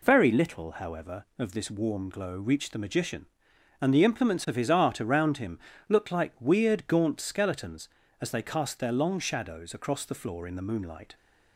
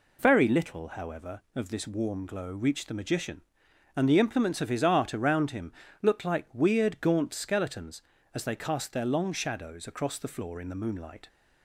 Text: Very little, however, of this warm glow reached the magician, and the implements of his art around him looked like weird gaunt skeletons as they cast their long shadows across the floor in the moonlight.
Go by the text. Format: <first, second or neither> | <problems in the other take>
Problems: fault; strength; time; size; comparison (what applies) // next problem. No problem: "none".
neither | pauses between "him" and "looked"; slight; the same in both